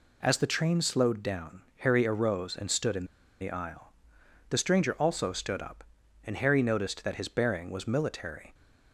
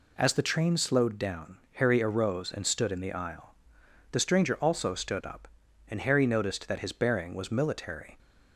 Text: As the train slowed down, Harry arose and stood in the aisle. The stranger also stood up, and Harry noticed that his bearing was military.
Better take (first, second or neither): second